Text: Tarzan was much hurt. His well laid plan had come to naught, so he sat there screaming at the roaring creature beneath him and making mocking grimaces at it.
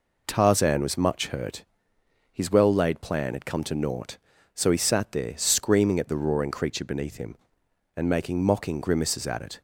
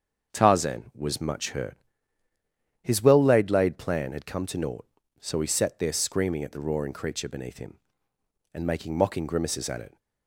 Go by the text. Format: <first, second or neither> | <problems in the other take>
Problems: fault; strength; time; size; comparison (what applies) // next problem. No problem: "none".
first | starts louder than the rest; until 1.3 s; 7 dB // says "laid" twice; at 3.4 s